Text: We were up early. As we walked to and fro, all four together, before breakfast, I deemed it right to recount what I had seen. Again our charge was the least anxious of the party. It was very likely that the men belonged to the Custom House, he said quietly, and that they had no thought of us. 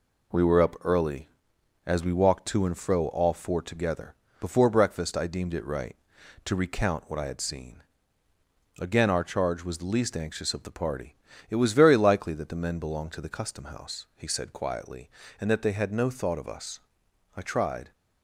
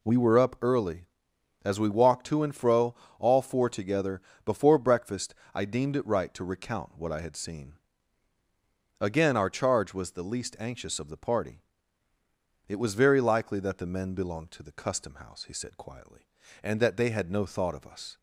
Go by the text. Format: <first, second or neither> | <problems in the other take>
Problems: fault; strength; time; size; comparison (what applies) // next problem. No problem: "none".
second | goes on to say "I tried"; from 17.3 s on; 0.56 s long